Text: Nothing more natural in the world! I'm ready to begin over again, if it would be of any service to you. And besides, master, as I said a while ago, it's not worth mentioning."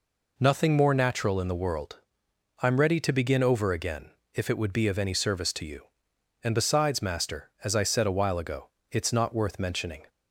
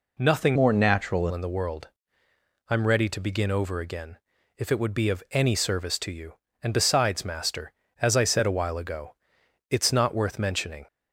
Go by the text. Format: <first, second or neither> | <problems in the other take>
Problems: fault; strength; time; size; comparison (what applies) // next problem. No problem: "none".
first | changes voice from "more" to "natural"; from 0.5 to 1.2 s; 0.7 s long